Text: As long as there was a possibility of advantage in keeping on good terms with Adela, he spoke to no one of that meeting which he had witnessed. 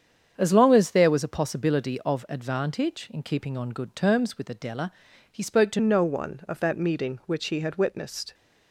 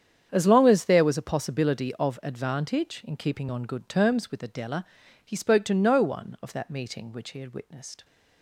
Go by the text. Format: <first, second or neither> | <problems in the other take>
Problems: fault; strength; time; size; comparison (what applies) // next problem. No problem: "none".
second | starts louder than the rest; strong; until 1.3 s; 7.5 dB; strong in the second // changes voice at "no"; from 5.7 s on; 2.6 s long